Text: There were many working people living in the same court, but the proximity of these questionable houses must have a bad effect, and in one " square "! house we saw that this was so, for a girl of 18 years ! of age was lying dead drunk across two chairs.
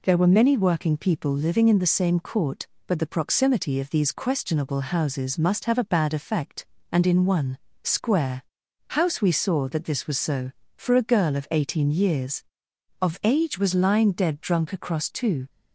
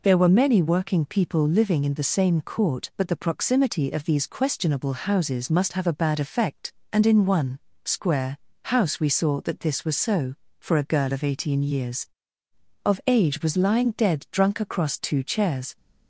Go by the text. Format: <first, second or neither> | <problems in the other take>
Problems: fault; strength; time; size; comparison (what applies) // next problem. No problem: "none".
second | stops before "chairs"; at 15.4 s